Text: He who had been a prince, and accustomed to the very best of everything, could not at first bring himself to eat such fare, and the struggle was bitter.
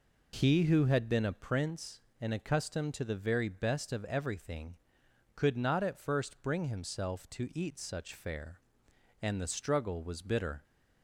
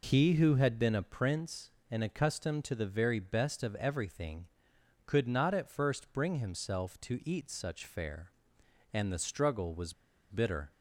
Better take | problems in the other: first | pauses between "was" and "bitter"; at 9.9 s; 0.36 s long

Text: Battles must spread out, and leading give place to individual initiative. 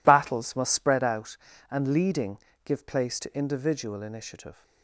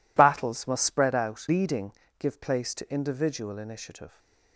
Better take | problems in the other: first | skips "and"; at 1.4 s // pauses between "leading" and "give"; slight; at 1.9 s; 0.26 s long; slight in the first

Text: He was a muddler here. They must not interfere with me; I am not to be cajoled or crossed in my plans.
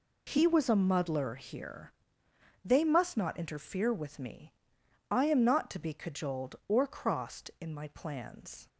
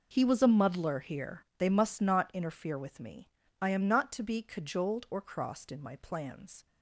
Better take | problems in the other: neither | none

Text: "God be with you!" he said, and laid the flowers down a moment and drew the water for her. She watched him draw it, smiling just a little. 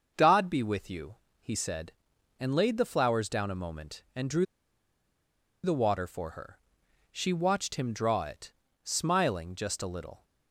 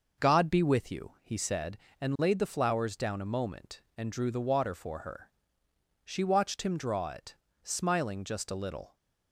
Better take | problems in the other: second | starts louder than the rest; until 1.1 s; 6.5 dB // pauses between "drew" and "the"; at 4.4 s; 1.1 s long

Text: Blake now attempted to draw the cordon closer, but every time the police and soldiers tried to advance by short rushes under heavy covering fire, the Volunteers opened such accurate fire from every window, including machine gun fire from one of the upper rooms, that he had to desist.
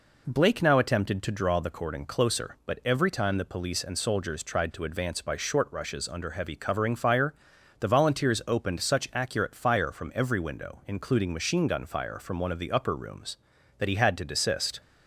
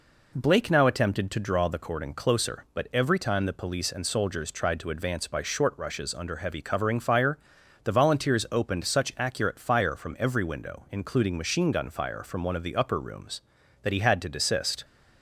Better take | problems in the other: neither | none

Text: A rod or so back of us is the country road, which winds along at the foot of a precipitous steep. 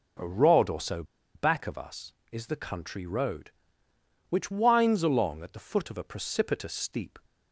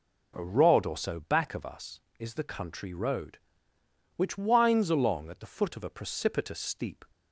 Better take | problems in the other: second | pauses between "so" and "back"; slight; at 1.0 s; 0.31 s long

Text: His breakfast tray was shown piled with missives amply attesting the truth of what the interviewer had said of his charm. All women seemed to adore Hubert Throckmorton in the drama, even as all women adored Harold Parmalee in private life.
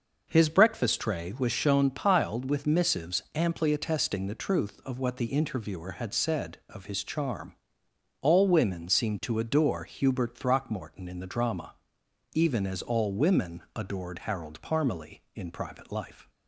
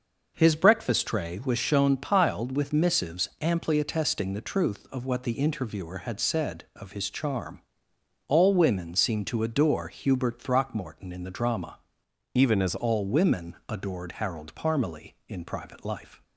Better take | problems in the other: first | changes voice from "even" to "as"; from 12.3 to 12.7 s; 0.4 s long

